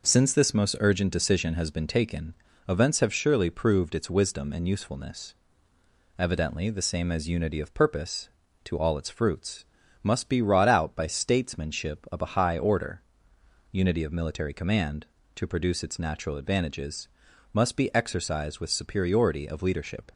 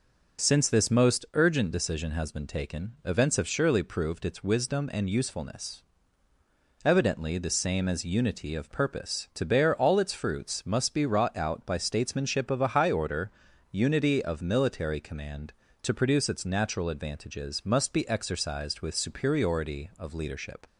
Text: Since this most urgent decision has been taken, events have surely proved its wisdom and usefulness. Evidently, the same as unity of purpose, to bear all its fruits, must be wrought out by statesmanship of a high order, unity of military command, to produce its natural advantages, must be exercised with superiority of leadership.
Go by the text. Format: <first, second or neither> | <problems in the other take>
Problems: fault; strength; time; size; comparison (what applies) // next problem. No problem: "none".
second | skips "bear"; at 8.7 s